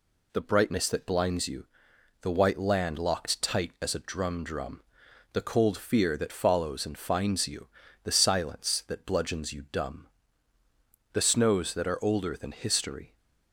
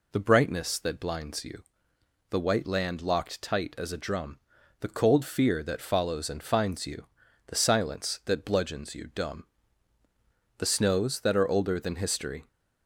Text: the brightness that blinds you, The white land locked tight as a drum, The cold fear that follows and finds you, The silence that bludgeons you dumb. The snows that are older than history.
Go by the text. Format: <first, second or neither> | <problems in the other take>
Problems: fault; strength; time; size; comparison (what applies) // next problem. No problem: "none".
second | says "drum" twice; at 4.4 s